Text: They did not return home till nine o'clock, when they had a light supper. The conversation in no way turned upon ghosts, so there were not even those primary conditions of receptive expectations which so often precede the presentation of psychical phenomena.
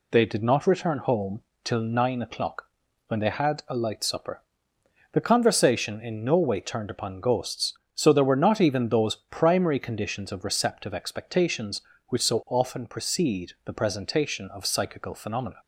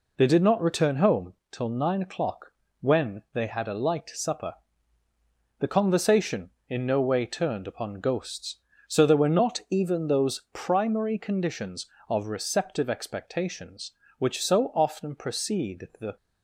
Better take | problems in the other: first | pauses between "home" and "till"; slight; at 1.3 s; 0.18 s long; slight in the first // stops before "presentation of psychical phenomena"; at 16.1 s

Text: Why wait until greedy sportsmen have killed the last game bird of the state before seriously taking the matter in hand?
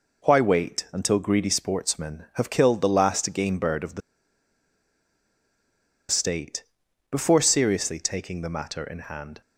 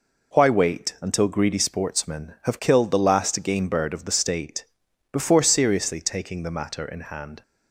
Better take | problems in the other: second | pauses between "the" and "state"; strong; at 4.0 s; 2.1 s long // pauses between "state" and "before"; noticeable; at 6.6 s; 0.46 s long; noticeable in the second

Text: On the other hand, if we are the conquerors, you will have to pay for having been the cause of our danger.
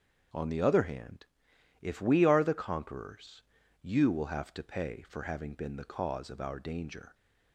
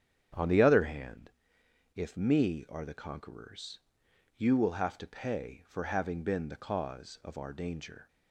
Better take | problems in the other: first | starts louder than the rest; strong; until 2.0 s; 8.5 dB; also in the first // says "me" for "we"; at 2.1 s

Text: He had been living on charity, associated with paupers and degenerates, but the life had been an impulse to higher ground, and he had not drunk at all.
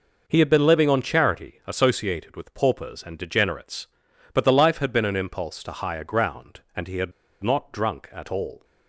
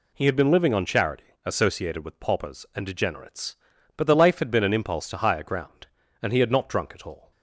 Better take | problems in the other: second | pauses between "had" and "not"; slight; at 7.1 s; 0.32 s long

